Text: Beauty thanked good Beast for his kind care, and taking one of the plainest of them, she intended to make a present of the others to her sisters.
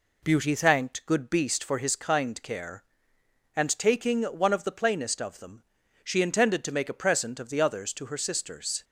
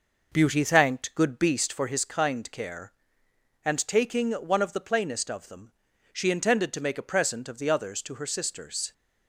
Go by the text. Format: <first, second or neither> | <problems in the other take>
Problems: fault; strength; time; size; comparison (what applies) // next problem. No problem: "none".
first | starts louder than the rest; noticeable; until 1.8 s; 5.5 dB